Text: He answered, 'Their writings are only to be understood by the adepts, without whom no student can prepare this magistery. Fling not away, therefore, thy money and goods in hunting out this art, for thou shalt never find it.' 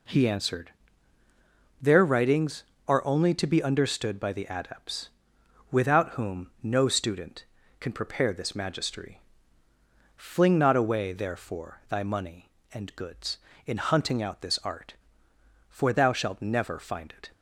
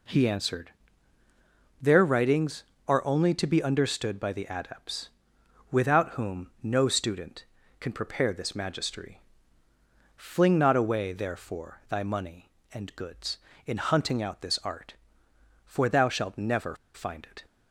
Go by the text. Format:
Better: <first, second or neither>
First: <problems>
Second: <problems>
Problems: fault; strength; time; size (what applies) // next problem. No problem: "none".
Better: first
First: none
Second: pauses between "never" and "find"; slight; at 16.7 s; 0.17 s long